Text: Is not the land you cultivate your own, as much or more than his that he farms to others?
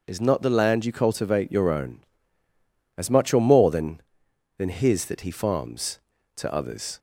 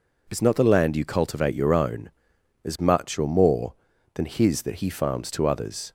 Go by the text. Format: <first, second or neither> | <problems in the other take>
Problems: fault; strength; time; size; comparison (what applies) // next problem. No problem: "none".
second | says "than" twice; at 4.5 s